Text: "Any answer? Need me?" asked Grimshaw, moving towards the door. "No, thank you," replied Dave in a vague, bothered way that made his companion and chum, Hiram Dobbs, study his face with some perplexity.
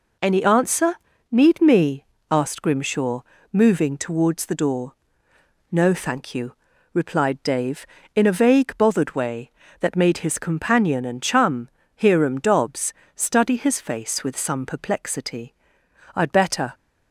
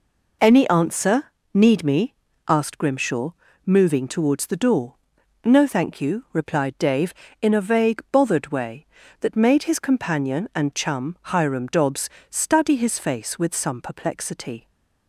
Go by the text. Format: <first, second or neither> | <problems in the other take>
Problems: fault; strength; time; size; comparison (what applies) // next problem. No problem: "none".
second | goes on to say "I'd better"; from 16.1 s on; 0.58 s long